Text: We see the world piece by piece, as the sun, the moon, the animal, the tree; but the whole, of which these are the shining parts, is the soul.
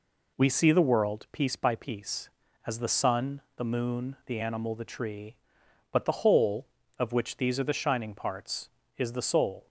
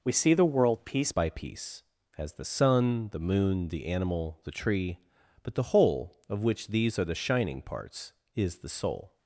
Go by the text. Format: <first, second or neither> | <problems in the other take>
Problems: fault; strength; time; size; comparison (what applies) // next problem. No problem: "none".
first | changes voice at "by"; from 1.1 s on; 8.0 s long